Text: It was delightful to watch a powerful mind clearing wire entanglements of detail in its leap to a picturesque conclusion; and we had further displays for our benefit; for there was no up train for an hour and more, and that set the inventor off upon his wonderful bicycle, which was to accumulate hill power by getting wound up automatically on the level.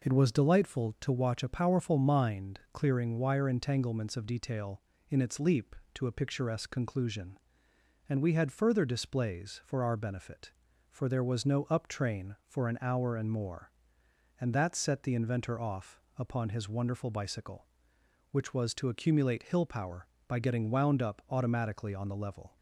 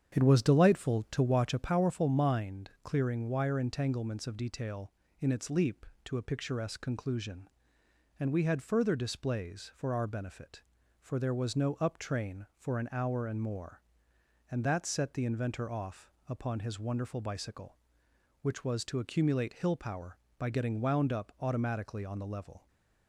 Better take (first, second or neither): first